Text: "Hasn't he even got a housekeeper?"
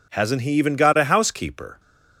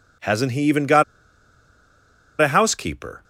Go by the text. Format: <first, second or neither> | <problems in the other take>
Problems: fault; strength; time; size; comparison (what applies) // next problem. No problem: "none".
first | pauses between "got" and "a"; strong; at 1.0 s; 1.3 s long